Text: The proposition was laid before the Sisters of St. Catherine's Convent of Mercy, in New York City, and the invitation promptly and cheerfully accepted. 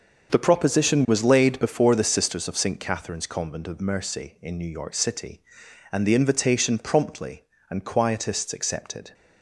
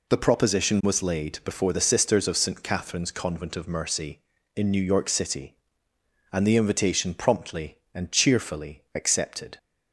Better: second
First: starts louder than the rest; until 1.3 s; 6.5 dB // says "quietists" for "cheerfully"; at 7.8 s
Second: none

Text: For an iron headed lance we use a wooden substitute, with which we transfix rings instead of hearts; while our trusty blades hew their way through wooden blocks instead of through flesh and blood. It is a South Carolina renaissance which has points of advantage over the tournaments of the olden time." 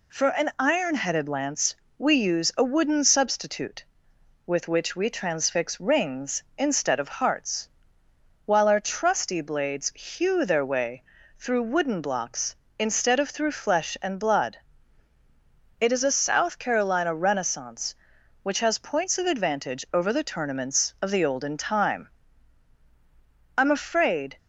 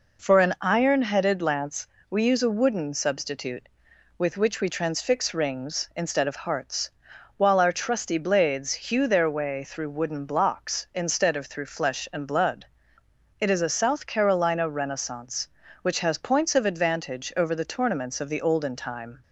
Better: second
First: pauses between "lance" and "we"; slight; at 1.7 s; 0.24 s long // pauses between "way" and "through"; slight; at 11.0 s; 0.36 s long // goes on to say "I'm afraid"; noticeable; from 23.5 s on; 0.80 s long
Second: pauses between "lance" and "we"; slight; at 1.8 s; 0.24 s long

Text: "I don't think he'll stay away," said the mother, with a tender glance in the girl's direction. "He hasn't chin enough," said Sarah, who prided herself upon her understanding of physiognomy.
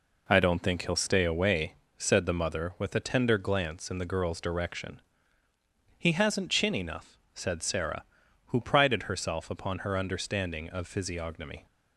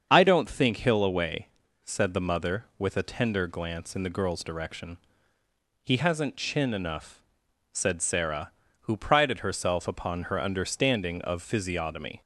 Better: first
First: none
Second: starts louder than the rest; strong; until 1.1 s; 7 dB // skips "stay"; at 1.0 s

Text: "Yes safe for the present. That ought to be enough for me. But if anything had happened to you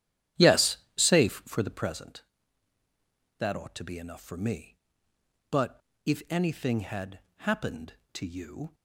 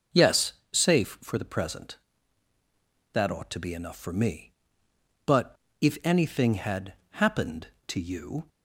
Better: second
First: starts louder than the rest; strong; until 1.9 s; 11 dB // pauses between "Yes" and "safe"; slight; at 0.7 s; 0.20 s long // pauses between "But" and "if"; slight; at 5.8 s; 0.24 s long // pauses between "had" and "happened"; slight; at 7.2 s; 0.18 s long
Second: pauses between "Yes" and "safe"; slight; at 0.5 s; 0.20 s long // pauses between "But" and "if"; slight; at 5.5 s; 0.24 s long // pauses between "had" and "happened"; slight; at 6.9 s; 0.18 s long

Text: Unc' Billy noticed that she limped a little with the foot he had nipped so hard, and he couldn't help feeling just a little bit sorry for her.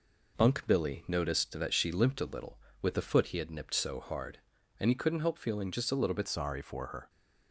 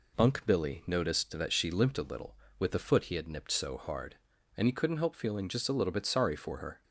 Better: second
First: changes voice at "sorry"; from 6.2 s on; 0.8 s long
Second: none

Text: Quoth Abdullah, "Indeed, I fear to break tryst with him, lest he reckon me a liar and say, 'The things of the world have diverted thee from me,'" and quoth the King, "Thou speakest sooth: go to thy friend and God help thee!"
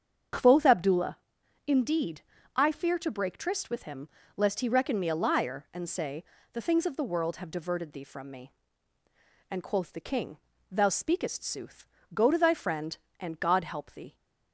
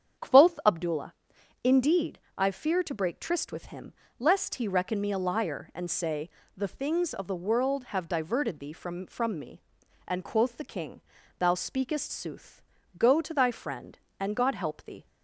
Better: first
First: starts louder than the rest; strong; until 1.9 s; 7.5 dB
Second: starts louder than the rest; strong; until 1.7 s; 8 dB // says "from" twice; at 9.0 s

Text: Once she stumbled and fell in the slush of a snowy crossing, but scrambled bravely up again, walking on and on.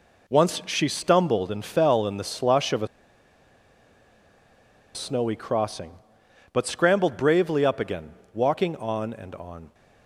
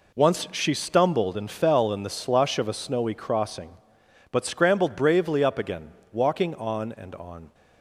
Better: second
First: pauses between "a" and "snowy"; strong; at 2.8 s; 2.0 s long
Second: none

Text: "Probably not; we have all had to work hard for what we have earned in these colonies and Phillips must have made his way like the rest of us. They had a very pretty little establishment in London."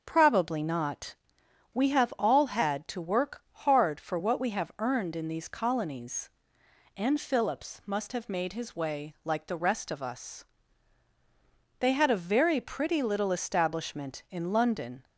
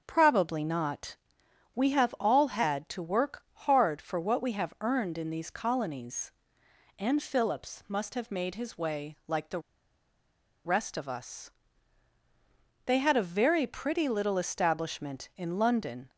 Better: first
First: starts louder than the rest; until 1.0 s; 6.5 dB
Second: starts louder than the rest; until 1.0 s; 7 dB // pauses between "the" and "rest"; at 9.6 s; 1.0 s long

